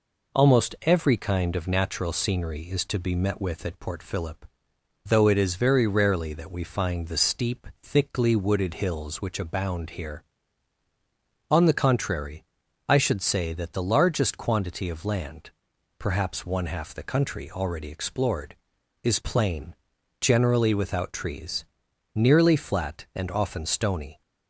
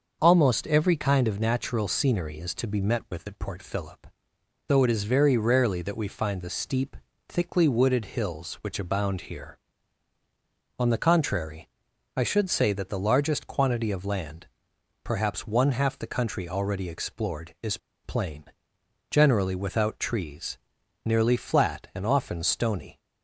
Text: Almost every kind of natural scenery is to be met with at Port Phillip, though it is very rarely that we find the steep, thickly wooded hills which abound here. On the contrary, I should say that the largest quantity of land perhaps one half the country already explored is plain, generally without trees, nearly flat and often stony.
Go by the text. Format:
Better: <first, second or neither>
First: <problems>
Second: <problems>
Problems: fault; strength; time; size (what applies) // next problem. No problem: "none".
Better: first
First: pauses between "land" and "perhaps"; noticeable; at 15.5 s; 0.48 s long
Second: starts louder than the rest; until 1.2 s; 6 dB // pauses between "land" and "perhaps"; noticeable; at 14.4 s; 0.58 s long // pauses between "is" and "plain"; slight; at 17.7 s; 0.27 s long